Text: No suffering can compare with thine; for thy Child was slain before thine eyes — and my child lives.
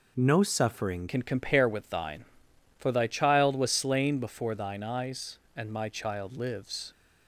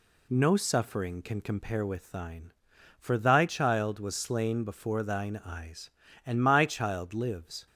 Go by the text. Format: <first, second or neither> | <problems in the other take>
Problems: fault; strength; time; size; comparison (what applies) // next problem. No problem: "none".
second | changes voice at "can"; from 1.0 s on; 5.9 s long